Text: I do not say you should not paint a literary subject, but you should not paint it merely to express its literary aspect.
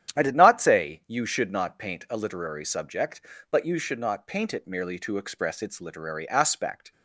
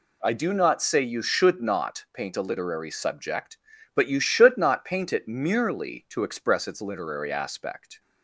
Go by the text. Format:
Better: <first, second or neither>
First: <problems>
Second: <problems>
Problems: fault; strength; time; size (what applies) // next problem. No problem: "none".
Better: second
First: starts louder than the rest; strong; until 1.2 s; 10.5 dB // says "did" for "do"; at 0.2 s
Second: none